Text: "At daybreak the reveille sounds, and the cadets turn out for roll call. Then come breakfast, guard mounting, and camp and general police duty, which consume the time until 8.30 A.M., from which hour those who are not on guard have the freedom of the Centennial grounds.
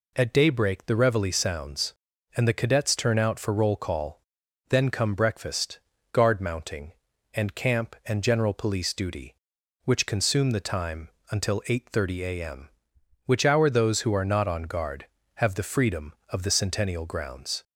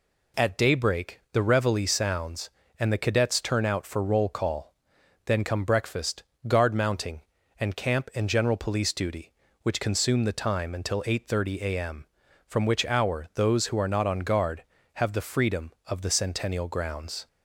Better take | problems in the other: second | pauses between "time" and "until"; slight; at 11.0 s; 0.22 s long // skips "from"; at 12.9 s

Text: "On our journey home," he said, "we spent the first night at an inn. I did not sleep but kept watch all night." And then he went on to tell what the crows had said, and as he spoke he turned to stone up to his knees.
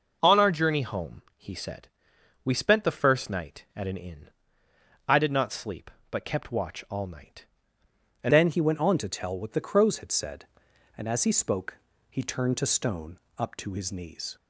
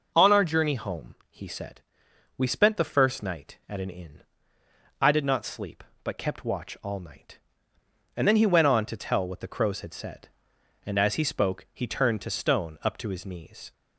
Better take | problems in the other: second | changes voice at "then"; from 8.3 s on; 6.0 s long // pauses between "spoke" and "he"; slight; at 11.7 s; 0.32 s long // pauses between "stone" and "up"; slight; at 13.1 s; 0.20 s long

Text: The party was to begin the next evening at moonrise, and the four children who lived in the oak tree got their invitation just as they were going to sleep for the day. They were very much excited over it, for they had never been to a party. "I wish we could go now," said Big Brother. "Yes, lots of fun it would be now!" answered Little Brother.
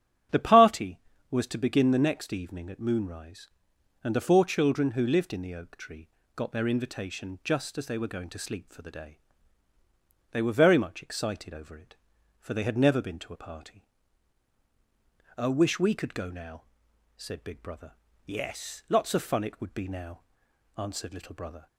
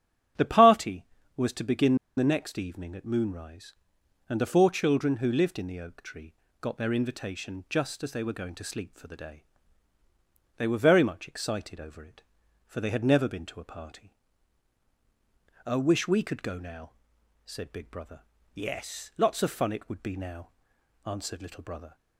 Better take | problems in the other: first | starts louder than the rest; strong; until 1.7 s; 9 dB; strong in the first // pauses between "begin" and "the"; slight; at 1.9 s; 0.21 s long // pauses between "tree" and "got"; slight; at 6.3 s; 0.28 s long; slight in the first

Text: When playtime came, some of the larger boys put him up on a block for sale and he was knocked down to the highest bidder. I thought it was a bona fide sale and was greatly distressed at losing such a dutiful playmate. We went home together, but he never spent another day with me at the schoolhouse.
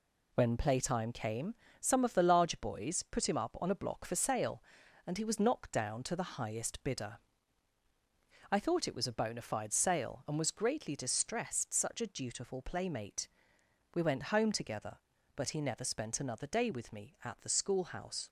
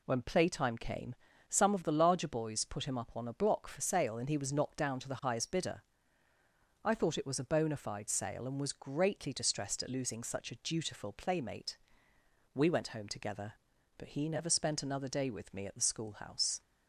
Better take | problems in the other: second | skips "at losing"; at 11.7 s

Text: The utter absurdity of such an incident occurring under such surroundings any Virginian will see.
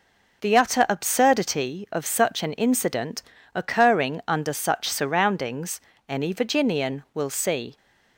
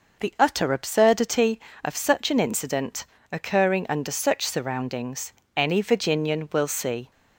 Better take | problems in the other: neither | pauses between "incident" and "occurring"; slight; the same in both // pauses between "surroundings" and "any"; slight; the same in both

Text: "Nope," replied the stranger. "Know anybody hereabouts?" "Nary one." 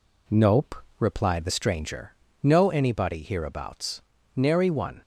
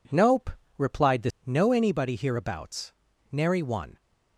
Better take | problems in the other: first | skips "stranger"; at 1.3 s

